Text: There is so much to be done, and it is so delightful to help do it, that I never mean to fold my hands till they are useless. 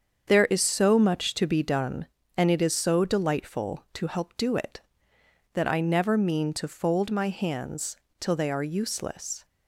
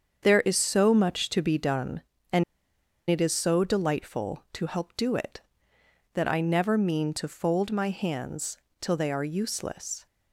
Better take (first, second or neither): first